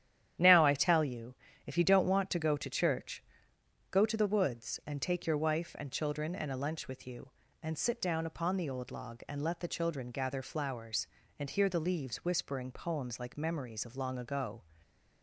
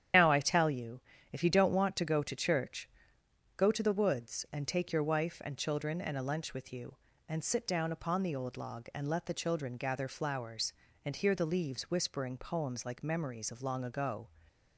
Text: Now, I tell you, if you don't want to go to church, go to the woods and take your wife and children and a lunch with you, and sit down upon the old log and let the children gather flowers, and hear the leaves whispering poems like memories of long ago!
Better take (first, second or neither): first